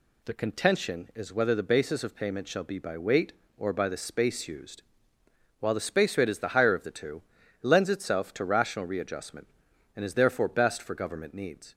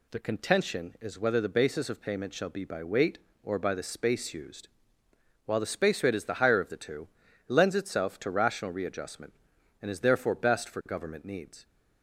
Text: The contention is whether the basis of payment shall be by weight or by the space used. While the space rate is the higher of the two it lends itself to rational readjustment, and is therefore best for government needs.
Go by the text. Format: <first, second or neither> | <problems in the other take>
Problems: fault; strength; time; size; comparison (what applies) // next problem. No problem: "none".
neither | pauses between "two" and "it"; the same in both